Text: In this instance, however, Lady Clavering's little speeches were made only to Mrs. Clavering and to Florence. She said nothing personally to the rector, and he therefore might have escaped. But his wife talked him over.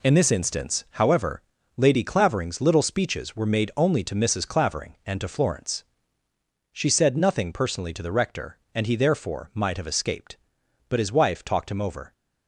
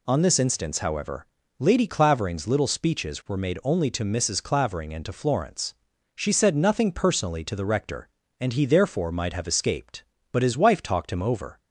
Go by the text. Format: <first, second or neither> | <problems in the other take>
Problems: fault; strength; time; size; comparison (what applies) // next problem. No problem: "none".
first | says "On" for "In"; at 0.0 s